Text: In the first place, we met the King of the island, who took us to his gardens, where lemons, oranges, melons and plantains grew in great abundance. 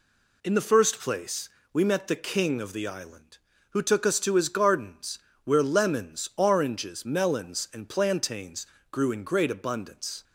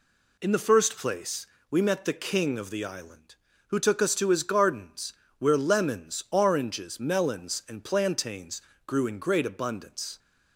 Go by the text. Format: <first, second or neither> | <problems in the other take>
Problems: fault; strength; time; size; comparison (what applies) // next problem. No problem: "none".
neither | pauses between "plantains" and "grew"; slight; the same in both